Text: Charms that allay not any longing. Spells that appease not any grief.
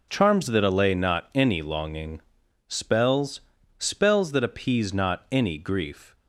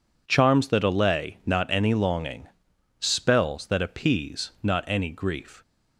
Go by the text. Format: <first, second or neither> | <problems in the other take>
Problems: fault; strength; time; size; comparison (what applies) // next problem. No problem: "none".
second | says "Spells" twice; at 3.7 s